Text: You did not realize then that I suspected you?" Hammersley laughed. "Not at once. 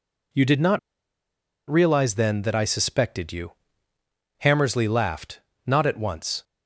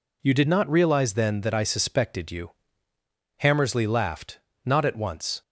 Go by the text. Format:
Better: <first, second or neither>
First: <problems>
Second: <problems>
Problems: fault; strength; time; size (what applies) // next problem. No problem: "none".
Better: second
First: pauses between "not" and "realize"; noticeable; at 0.7 s; 0.89 s long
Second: none